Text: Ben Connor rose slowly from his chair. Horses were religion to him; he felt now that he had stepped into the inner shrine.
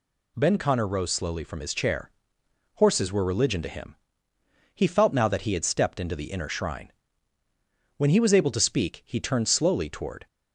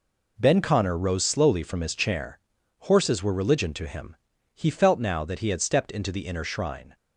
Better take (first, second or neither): second